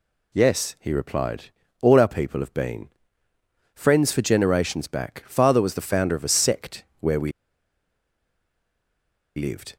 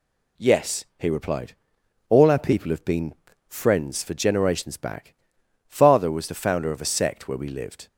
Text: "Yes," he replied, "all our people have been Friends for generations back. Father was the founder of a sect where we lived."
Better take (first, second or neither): second